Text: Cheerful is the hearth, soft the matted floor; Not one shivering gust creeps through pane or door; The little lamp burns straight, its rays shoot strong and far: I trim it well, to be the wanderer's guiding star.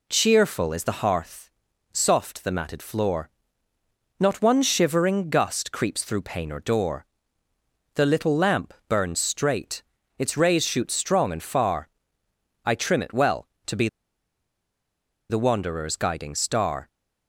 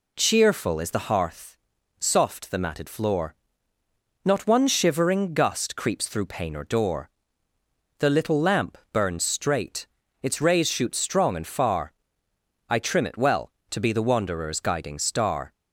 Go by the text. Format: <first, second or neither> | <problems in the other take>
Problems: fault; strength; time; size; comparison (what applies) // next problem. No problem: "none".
second | pauses between "lamp" and "burns"; slight; at 8.7 s; 0.16 s long; slight in the second // pauses between "be" and "the"; strong; at 13.8 s; 1.4 s long